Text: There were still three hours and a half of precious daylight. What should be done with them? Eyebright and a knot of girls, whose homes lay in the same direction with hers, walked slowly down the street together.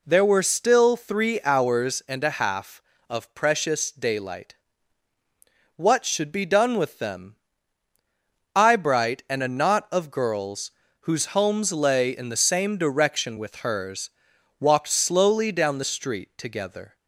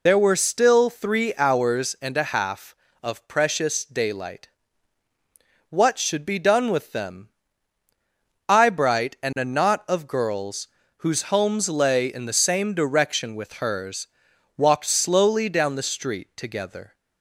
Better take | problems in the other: first | loses the start of "There"; at 0.0 s; 70 ms

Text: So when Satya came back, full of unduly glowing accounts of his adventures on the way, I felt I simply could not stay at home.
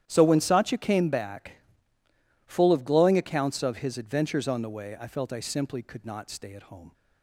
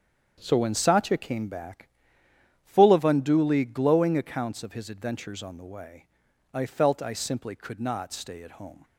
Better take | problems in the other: second | starts louder than the rest; strong; until 1.0 s; 11 dB; strong in the second // skips "unduly"; at 2.8 s

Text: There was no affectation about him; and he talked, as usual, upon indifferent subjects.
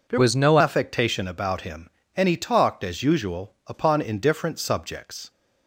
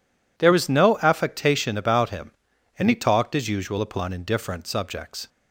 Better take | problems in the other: second | changes voice from "was" to "no"; from 0.1 to 0.5 s; 0.4 s long

